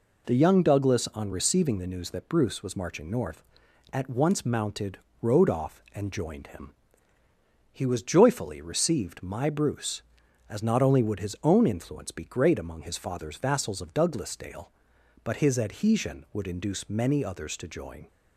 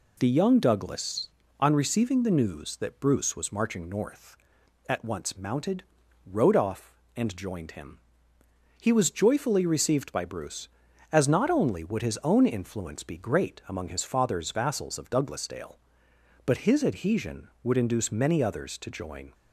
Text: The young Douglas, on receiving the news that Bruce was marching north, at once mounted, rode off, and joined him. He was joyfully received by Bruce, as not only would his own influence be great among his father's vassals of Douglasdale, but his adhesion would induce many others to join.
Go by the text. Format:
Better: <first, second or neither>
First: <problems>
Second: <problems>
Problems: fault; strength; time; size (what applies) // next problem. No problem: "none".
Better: second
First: says "my" for "by"; at 9.2 s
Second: none